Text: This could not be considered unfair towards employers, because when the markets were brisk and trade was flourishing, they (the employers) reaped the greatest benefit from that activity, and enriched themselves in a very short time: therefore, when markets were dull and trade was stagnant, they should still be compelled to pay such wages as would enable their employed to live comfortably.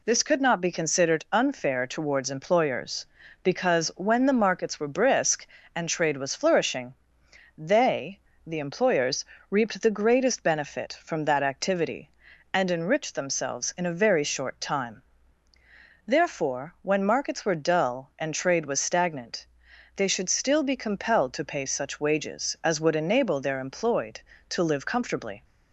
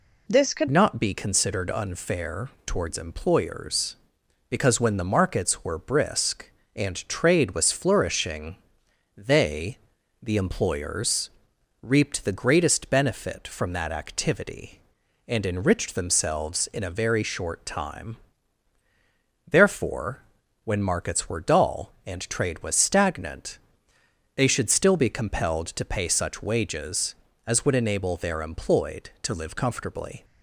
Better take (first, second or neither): first